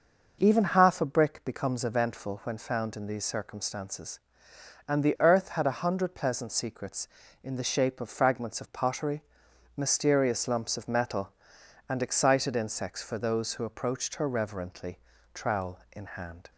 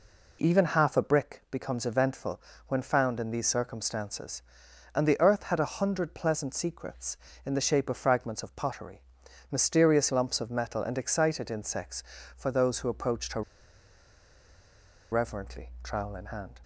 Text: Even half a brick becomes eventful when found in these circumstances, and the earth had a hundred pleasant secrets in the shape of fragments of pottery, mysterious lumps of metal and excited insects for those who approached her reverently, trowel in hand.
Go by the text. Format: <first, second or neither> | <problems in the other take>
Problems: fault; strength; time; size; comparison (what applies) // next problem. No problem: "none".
first | pauses between "eventful" and "when"; slight; at 2.3 s; 0.28 s long // pauses between "her" and "reverently"; strong; at 13.4 s; 1.6 s long